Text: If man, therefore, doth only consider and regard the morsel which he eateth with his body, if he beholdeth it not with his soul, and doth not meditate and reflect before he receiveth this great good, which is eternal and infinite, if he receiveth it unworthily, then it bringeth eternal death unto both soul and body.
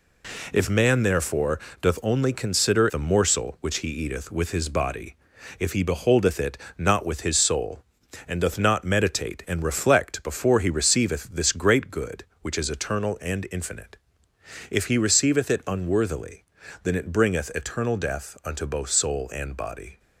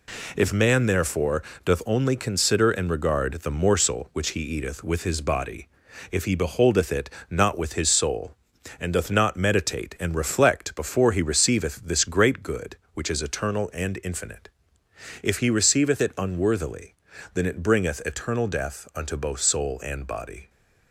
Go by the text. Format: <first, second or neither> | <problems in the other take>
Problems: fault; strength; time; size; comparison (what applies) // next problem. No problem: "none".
second | skips "and regard"; at 2.8 s // pauses between "it" and "not"; slight; at 6.5 s; 0.20 s long; slight in the second